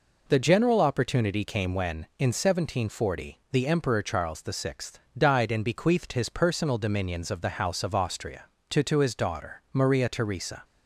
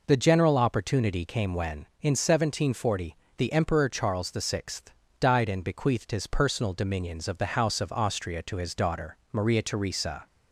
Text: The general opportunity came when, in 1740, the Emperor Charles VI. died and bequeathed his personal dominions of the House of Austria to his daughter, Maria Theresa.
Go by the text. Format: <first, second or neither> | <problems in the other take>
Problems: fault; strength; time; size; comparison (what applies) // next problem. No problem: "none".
second | says "to" twice; at 8.8 s